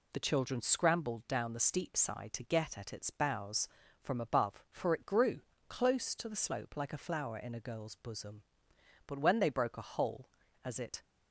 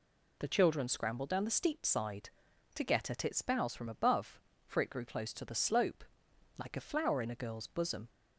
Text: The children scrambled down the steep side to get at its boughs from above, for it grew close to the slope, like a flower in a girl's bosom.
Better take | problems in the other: second | pauses between "grew" and "close"; slight; at 5.4 s; 0.28 s long // goes on to say "But when they broke a hole as it"; strong; from 9.0 s on; 1.9 s long

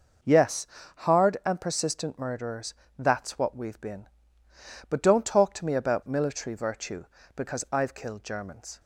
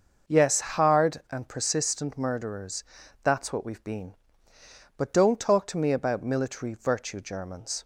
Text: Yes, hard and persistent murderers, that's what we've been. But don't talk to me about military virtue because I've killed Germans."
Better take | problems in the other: first | starts louder than the rest; noticeable; until 1.4 s; 6 dB // skips "because I've killed"; at 7.1 s

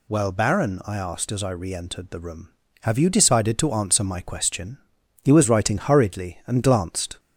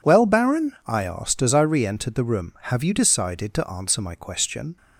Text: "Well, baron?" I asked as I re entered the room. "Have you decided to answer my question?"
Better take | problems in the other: second | goes on to say "He was writing hurriedly and glanced"; strong; from 5.2 s on; 1.9 s long

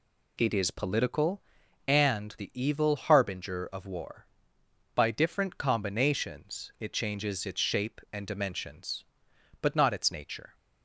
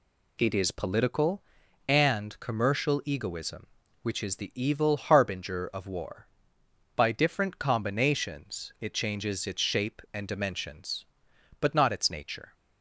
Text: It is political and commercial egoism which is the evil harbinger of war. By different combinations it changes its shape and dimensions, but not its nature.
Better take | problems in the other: second | skips "commercial egoism which is"; at 2.3 s

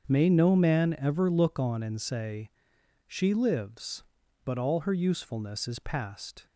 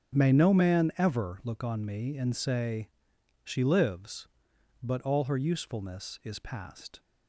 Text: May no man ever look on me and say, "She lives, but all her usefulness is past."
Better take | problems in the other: second | starts louder than the rest; until 1.1 s; 7 dB; strong in the second // skips "me"; at 1.8 s

